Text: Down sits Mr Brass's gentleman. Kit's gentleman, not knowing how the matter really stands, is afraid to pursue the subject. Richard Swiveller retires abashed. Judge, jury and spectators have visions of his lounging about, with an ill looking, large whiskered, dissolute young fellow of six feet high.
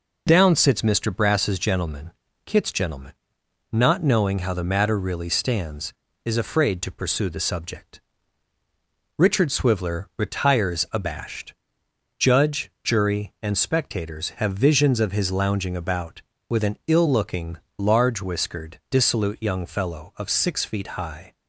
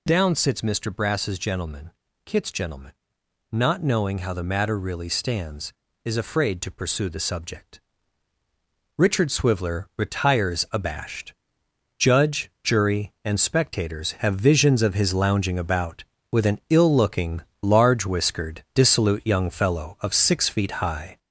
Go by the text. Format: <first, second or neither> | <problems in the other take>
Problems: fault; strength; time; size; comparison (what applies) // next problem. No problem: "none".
first | gets louder; noticeable; throughout; 5 dB